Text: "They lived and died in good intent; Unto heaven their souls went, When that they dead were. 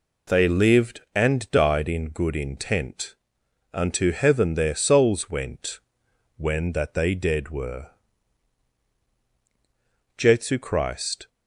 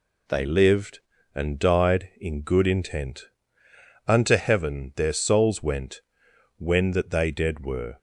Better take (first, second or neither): second